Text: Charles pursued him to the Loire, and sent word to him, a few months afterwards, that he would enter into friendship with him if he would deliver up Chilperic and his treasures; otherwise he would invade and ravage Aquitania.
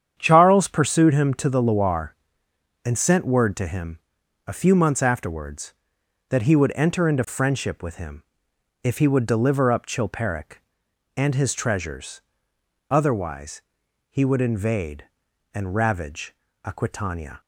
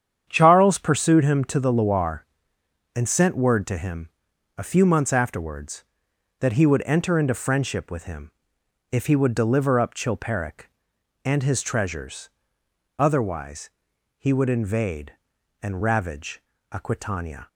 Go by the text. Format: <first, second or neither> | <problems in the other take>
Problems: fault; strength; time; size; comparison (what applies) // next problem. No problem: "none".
neither | starts louder than the rest; strong; the same in both // pauses between "him" and "if"; noticeable; the same in both // pauses between "otherwise" and "he"; noticeable; the same in both // pauses between "ravage" and "Aquitania"; slight; the same in both